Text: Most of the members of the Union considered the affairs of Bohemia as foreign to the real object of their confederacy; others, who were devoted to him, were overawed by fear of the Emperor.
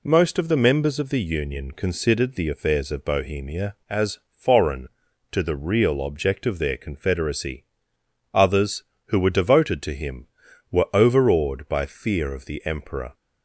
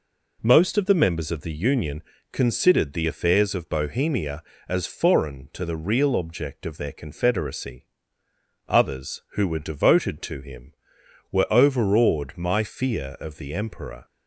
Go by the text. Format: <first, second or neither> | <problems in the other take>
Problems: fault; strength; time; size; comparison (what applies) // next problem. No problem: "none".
first | pauses between "Union" and "considered"; slight; at 2.0 s; 0.30 s long // says "my" for "by"; at 12.3 s